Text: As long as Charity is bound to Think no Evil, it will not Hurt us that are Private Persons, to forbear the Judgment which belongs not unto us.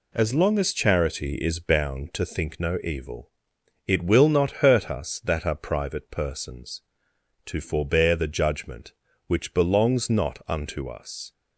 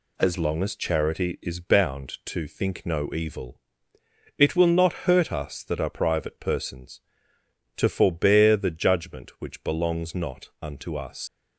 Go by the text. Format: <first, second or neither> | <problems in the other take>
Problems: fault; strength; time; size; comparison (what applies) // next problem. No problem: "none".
first | leaves "us" unfinished; at 11.2 s; 120 ms